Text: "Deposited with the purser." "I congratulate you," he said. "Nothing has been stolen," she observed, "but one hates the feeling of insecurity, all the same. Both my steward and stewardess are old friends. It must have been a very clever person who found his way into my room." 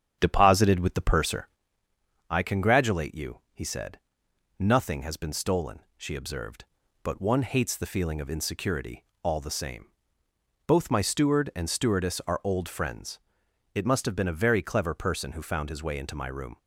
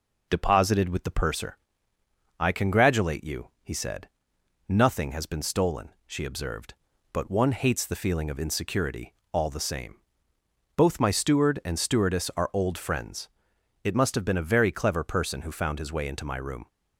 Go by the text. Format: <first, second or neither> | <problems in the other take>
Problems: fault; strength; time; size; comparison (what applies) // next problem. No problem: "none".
second | starts louder than the rest; strong; until 1.6 s; 9 dB